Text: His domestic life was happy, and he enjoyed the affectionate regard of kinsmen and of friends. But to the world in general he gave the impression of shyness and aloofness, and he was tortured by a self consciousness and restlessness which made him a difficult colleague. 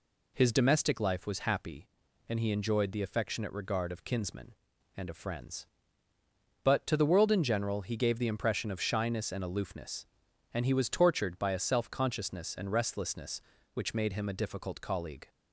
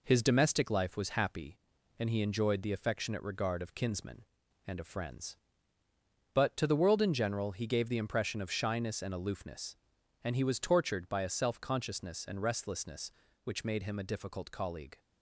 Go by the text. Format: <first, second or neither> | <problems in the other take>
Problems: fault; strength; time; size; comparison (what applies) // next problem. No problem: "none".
first | gets quieter; noticeable; throughout; 4 dB